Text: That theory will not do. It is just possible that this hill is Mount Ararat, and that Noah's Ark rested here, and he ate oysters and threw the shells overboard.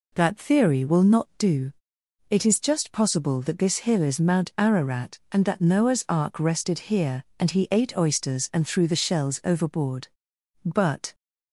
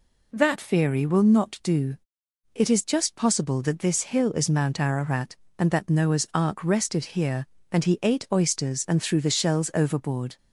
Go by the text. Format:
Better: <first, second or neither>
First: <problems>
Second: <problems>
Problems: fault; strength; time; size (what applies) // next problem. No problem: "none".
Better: second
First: goes on to say "But"; slight; from 10.6 s on; 0.48 s long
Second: none